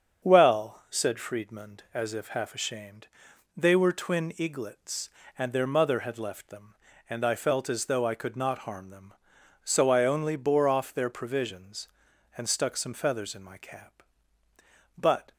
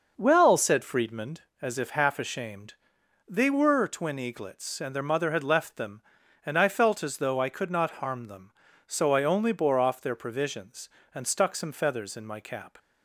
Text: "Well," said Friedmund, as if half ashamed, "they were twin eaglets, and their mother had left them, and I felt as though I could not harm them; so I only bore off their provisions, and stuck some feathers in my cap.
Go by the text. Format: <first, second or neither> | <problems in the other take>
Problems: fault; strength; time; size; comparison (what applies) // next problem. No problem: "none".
second | starts louder than the rest; strong; until 1.2 s; 7.5 dB // goes on to say "But"; slight; from 14.9 s on; 0.36 s long